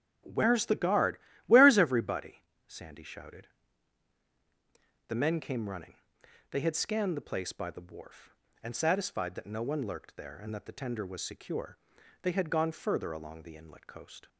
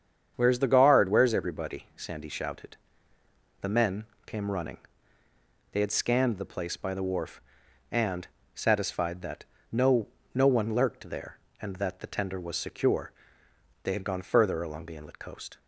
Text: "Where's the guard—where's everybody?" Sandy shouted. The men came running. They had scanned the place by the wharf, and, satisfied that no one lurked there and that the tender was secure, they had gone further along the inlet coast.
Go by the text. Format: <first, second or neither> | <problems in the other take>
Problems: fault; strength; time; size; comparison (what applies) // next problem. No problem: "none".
first | starts louder than the rest; strong; until 1.3 s; 8 dB; strong in the first // pauses between "men" and "came"; slight; at 4.0 s; 0.20 s long // pauses between "that" and "no"; slight; at 9.4 s; 0.26 s long // says "no" twice; at 10.3 s